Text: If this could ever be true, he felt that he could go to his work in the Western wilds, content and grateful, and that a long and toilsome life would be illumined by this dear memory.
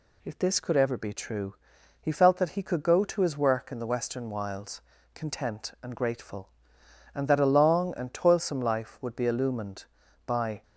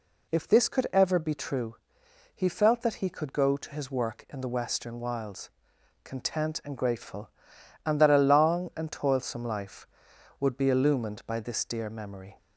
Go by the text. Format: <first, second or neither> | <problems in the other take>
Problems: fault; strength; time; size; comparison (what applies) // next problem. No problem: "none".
second | stops before "this dear memory"; at 10.6 s